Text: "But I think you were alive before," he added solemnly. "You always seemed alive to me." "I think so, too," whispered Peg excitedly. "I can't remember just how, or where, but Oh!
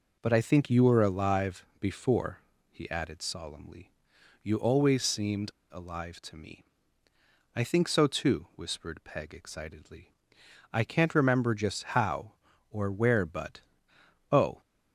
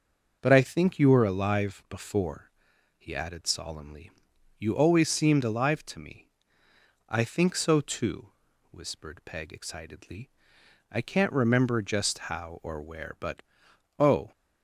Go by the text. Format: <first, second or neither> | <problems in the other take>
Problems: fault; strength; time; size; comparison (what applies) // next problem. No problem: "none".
second | pauses between "seemed" and "alive"; slight; at 5.5 s; 0.20 s long // pauses between "but" and "Oh"; noticeable; at 13.6 s; 0.68 s long; noticeable in the second